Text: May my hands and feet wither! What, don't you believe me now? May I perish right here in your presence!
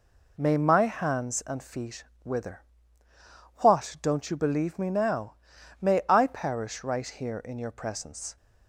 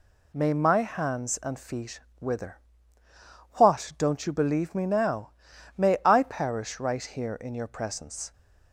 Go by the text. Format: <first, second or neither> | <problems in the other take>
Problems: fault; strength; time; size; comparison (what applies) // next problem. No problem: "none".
second | starts louder than the rest; until 1.3 s; 3.5 dB // pauses between "feet" and "wither"; slight; at 2.0 s; 0.20 s long; slight in the second